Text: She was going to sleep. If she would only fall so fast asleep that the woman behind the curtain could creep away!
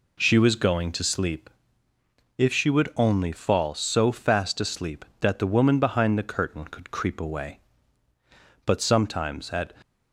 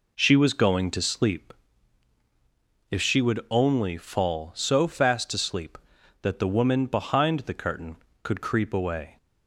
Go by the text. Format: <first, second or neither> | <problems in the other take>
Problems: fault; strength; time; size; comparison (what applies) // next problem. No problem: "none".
second | goes on to say "But sometimes at"; noticeable; from 8.6 s on; 1.0 s long